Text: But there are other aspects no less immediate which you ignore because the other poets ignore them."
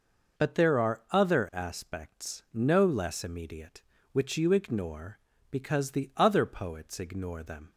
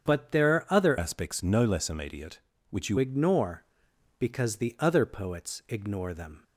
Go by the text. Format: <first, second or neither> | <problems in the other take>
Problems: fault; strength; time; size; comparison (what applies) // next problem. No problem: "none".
first | starts louder than the rest; strong; until 1.1 s; 8 dB // changes voice from "aspects" to "you"; from 0.9 to 2.9 s; 2.0 s long